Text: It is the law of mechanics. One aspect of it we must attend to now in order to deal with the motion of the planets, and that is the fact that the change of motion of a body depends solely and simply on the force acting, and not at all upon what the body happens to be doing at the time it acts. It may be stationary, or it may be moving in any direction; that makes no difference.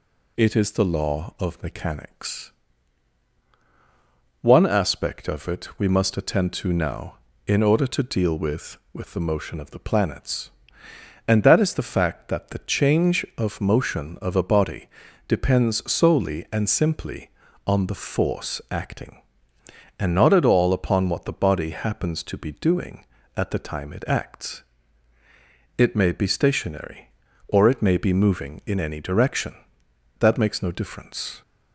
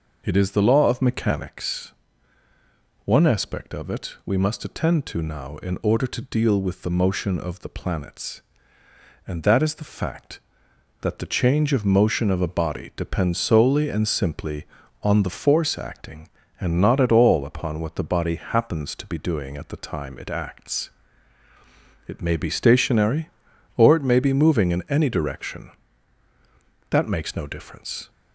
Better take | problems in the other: second | says "with" twice; at 8.9 s // pauses between "body" and "depends"; at 14.8 s; 0.40 s long

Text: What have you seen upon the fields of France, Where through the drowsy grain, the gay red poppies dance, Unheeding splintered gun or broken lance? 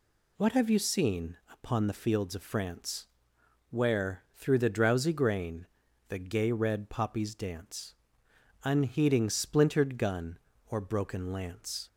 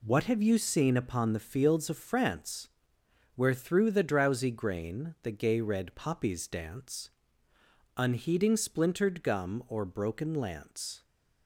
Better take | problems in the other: first | says "gum" for "gun"; at 9.2 s

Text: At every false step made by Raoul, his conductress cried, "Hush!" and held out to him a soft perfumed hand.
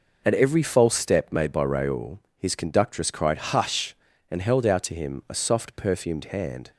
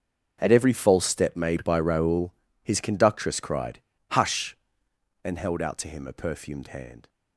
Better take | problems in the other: first | starts louder than the rest; noticeable; until 1.4 s; 6 dB // skips "soft"; at 6.1 s

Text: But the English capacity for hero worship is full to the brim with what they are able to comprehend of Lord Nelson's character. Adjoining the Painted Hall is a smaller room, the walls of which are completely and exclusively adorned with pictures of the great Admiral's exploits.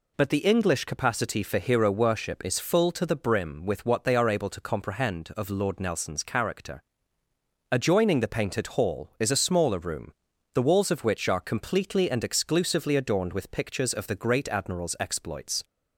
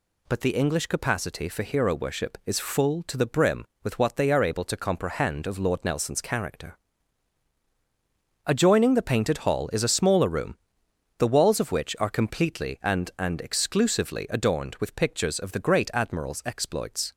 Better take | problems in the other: first | says "and" twice; at 13.1 s

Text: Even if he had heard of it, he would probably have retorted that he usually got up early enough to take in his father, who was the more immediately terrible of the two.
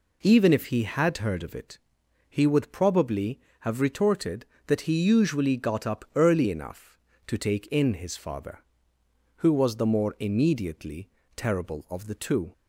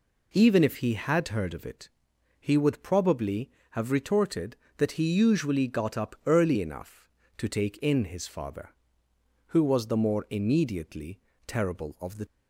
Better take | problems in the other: first | pauses between "immediately" and "terrible"; slight; at 11.1 s; 0.28 s long; slight in the first // stops before "two"; at 12.2 s

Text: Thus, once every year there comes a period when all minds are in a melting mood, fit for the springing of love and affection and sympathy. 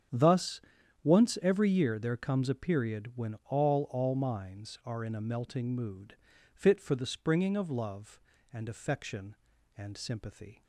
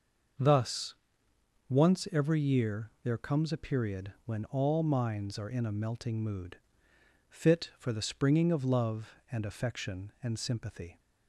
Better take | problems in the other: second | starts louder than the rest; strong; until 1.5 s; 8 dB // says "all" twice; at 3.9 s

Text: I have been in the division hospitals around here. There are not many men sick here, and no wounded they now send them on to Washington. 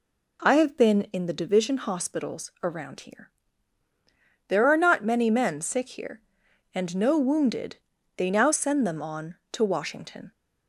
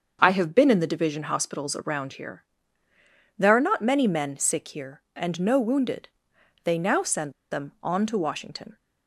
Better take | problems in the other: first | starts louder than the rest; until 1.2 s; 6.5 dB // pauses between "wounded" and "they"; noticeable; at 6.0 s; 0.56 s long; also in the first // pauses between "send" and "them"; slight; at 7.3 s; 0.19 s long

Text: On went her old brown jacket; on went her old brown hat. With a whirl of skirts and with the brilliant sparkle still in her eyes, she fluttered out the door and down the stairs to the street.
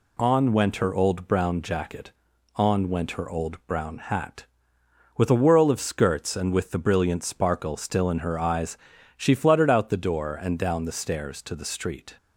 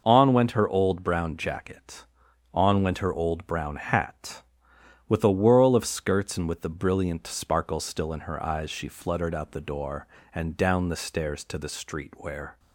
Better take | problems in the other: first | goes on to say "Where"; slight; from 12.1 s on; 0.44 s long

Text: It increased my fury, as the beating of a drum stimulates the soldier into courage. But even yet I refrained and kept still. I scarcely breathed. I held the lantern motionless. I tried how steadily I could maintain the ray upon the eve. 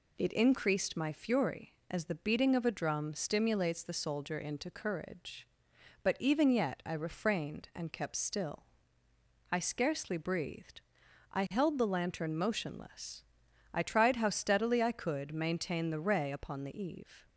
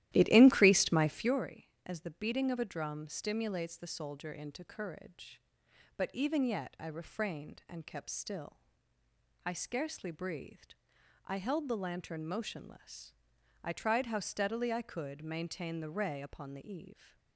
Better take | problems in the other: first | starts louder than the rest; strong; until 1.4 s; 14 dB

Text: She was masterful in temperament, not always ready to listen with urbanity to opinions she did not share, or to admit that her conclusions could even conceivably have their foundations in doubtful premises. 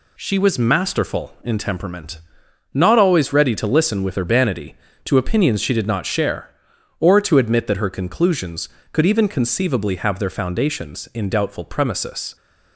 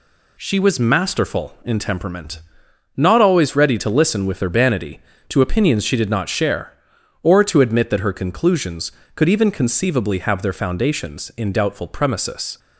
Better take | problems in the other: neither | none

